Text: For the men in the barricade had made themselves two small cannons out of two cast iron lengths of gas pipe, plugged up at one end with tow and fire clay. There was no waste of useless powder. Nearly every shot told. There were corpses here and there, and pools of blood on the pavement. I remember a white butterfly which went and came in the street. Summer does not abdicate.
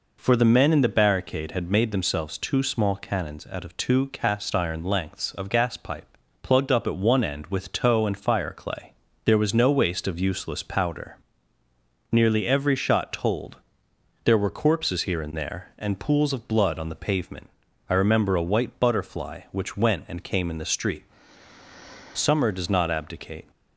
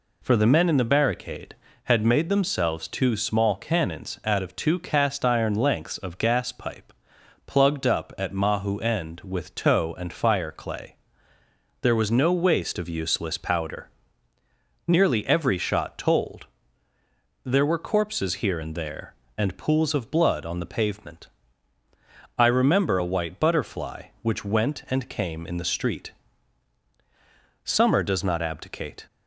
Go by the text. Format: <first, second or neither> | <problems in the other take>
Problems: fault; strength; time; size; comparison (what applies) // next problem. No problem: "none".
first | says "mahu" for "one"; at 8.3 s